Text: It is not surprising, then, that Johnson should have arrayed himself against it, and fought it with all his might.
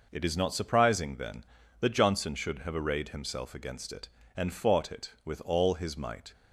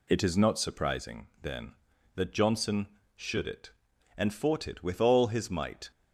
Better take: first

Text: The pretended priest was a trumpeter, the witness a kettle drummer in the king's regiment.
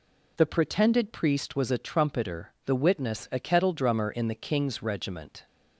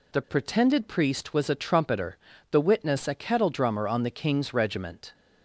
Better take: first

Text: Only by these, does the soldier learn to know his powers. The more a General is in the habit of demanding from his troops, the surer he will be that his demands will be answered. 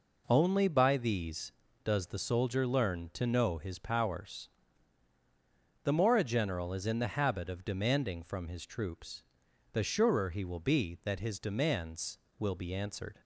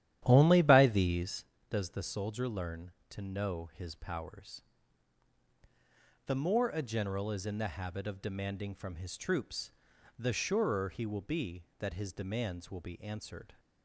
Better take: first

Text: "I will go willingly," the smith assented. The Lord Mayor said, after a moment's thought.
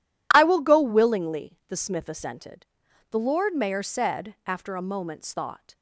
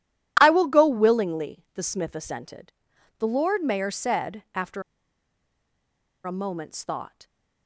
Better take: first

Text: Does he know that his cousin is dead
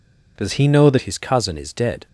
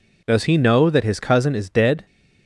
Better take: second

